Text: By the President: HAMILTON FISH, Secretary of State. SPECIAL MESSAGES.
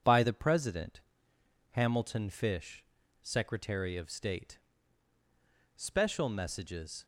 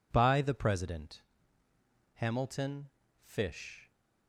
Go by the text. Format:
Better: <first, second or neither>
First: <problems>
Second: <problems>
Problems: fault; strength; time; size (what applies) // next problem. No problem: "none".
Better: first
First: none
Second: pauses between "HAMILTON" and "FISH"; slight; at 2.8 s; 0.32 s long // stops before "Secretary of State SPECIAL MESSAGES"; at 3.9 s